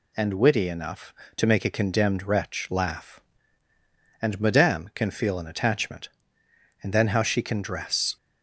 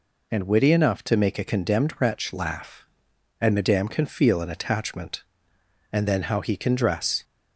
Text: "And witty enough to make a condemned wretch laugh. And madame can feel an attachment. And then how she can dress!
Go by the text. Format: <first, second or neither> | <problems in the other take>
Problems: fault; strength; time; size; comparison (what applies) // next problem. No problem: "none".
first | says "he" for "she"; at 6.4 s